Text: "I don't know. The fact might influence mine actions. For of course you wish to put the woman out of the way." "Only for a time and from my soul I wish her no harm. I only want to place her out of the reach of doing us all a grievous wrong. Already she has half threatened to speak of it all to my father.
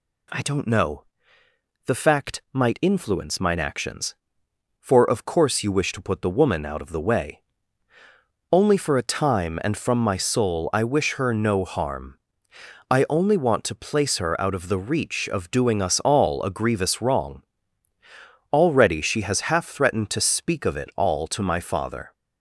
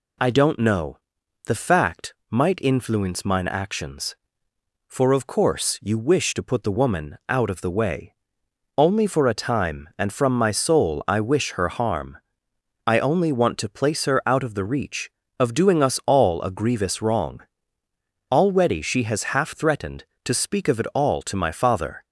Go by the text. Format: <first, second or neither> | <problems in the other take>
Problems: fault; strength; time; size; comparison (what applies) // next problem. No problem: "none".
first | pauses between "fact" and "might"; slight; at 2.1 s; 0.16 s long // skips "no"; at 11.6 s